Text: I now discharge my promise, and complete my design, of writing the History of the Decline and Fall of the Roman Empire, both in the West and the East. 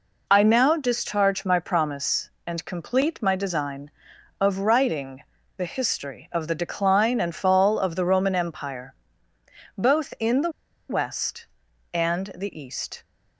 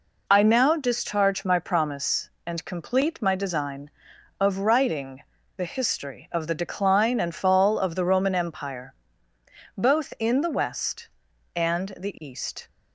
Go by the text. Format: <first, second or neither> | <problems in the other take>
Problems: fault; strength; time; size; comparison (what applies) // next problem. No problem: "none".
second | pauses between "writing" and "the"; slight; at 5.2 s; 0.32 s long; slight in the second // pauses between "the" and "West"; at 10.5 s; 0.38 s long